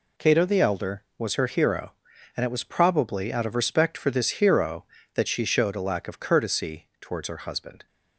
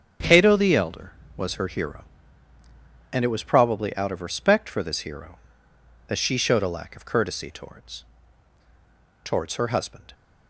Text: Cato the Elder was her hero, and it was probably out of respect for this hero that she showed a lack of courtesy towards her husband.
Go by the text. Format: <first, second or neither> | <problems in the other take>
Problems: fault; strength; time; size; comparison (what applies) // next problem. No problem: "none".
first | starts louder than the rest; strong; until 1.4 s; 8.5 dB // says "towards" twice; at 9.2 s